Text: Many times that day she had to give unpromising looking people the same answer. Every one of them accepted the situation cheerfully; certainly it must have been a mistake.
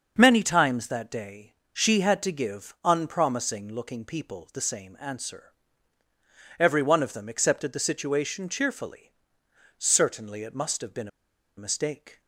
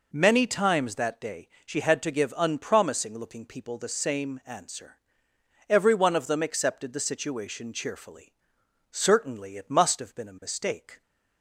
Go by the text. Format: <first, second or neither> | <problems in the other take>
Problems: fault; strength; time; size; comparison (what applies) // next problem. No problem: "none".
second | starts louder than the rest; until 1.1 s; 6.5 dB // pauses between "day" and "she"; slight; at 1.5 s; 0.20 s long; slight in the second // pauses between "been" and "a"; noticeable; at 11.0 s; 0.50 s long